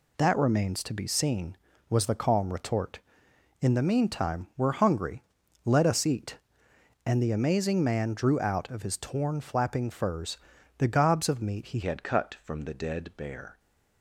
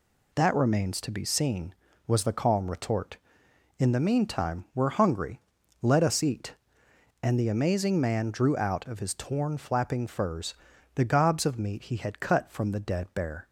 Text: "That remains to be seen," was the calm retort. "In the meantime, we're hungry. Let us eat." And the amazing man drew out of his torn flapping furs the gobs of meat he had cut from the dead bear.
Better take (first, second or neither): second